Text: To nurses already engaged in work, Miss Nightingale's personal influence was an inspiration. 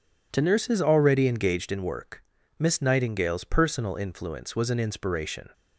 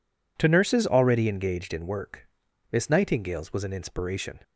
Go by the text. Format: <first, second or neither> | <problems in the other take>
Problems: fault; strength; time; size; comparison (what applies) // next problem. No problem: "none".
first | skips "personal influence"; at 3.5 s